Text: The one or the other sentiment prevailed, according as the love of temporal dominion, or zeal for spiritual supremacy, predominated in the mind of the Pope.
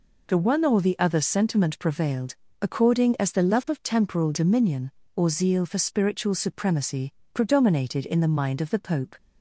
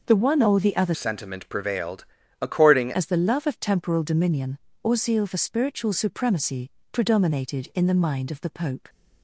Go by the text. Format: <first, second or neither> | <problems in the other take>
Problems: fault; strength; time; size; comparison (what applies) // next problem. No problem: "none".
first | changes voice from "sentiment" to "according"; from 0.9 to 2.9 s; 2.0 s long